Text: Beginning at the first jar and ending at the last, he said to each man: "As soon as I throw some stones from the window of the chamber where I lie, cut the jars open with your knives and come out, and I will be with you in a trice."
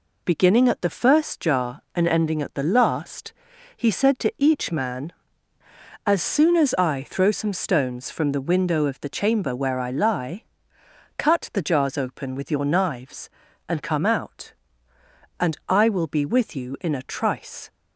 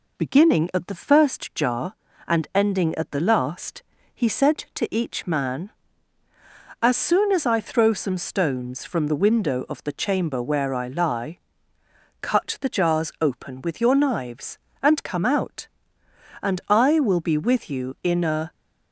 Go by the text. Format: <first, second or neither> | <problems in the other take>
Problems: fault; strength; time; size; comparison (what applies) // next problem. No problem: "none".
first | stops before "trice"; at 18.5 s